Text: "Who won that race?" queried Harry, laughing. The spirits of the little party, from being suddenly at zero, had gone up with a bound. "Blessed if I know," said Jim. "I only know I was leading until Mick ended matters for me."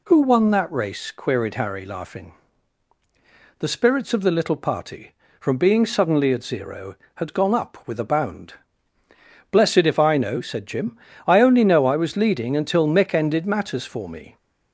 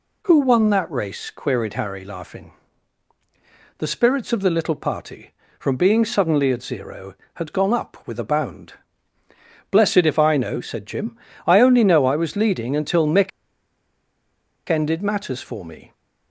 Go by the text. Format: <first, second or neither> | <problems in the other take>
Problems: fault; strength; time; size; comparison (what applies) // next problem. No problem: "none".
first | pauses between "Mick" and "ended"; strong; at 13.3 s; 1.3 s long